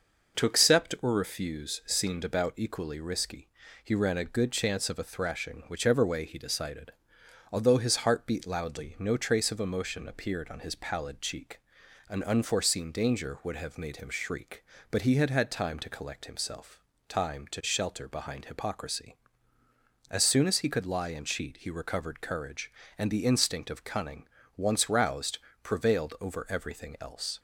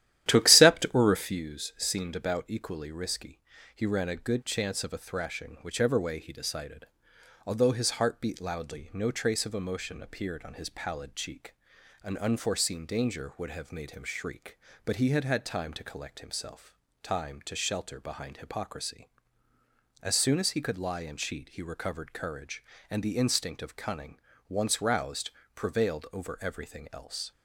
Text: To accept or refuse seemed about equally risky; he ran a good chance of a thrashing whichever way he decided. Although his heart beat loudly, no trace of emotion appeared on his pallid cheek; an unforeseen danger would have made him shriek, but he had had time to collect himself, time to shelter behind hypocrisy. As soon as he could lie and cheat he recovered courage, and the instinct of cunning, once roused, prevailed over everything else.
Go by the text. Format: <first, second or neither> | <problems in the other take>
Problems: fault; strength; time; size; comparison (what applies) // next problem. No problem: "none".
first | starts louder than the rest; strong; until 1.4 s; 12.5 dB